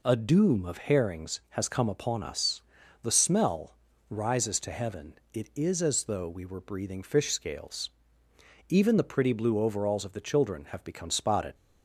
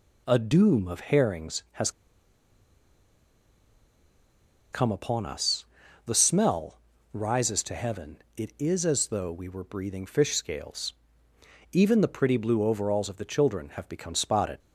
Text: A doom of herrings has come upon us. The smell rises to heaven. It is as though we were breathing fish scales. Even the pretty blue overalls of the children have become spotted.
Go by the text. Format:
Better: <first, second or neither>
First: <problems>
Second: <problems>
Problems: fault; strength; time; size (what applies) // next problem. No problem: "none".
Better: first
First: pauses between "smell" and "rises"; slight; at 3.7 s; 0.34 s long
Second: pauses between "has" and "come"; strong; at 1.9 s; 2.8 s long // pauses between "smell" and "rises"; slight; at 6.7 s; 0.34 s long